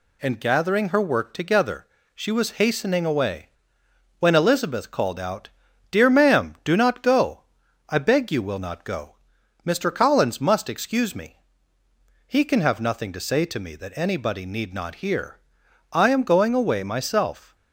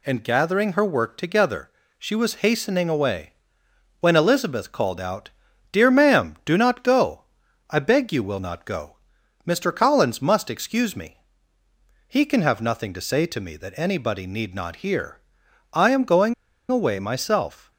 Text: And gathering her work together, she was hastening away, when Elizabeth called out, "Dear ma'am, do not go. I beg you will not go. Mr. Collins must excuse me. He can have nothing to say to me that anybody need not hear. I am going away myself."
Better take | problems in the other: first | pauses between "going" and "away"; slight; at 16.3 s; 0.35 s long

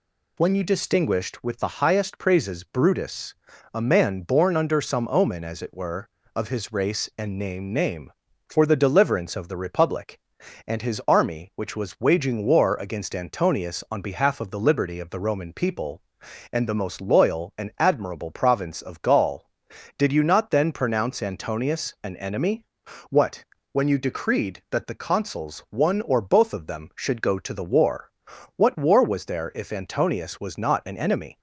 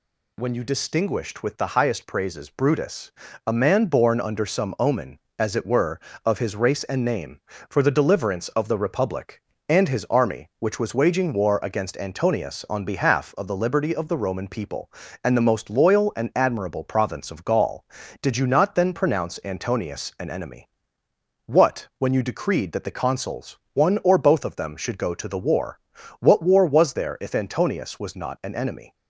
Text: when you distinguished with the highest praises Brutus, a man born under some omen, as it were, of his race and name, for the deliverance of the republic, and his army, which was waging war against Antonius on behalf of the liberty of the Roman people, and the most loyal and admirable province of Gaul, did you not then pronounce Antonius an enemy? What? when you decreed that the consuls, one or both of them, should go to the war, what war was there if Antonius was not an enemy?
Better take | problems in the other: second | says "name" twice; at 7.7 s

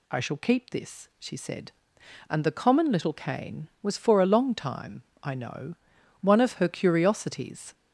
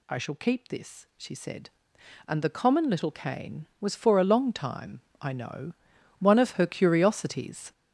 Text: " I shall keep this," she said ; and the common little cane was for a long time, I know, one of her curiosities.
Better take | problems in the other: first | gets louder; strong; throughout; 9 dB

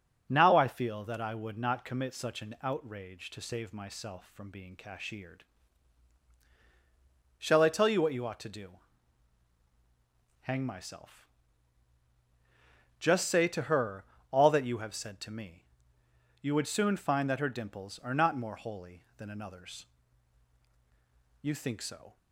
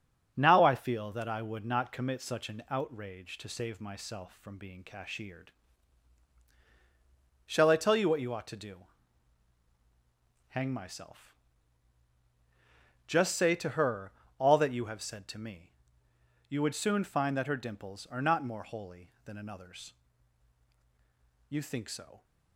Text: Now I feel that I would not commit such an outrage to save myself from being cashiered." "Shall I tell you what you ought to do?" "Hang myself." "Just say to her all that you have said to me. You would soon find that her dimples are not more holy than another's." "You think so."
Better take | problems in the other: first | gets quieter; noticeable; throughout; 4.5 dB // starts louder than the rest; strong; until 1.3 s; 7.5 dB; also in the first // pauses between "her" and "all"; slight; at 14.1 s; 0.26 s long; slight in the first

